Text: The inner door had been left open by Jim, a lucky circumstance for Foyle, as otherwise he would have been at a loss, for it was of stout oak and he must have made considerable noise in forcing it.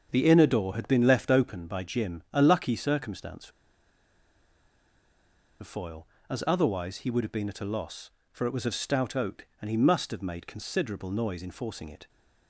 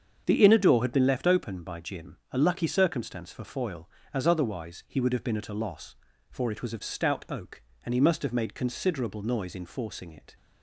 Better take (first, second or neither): second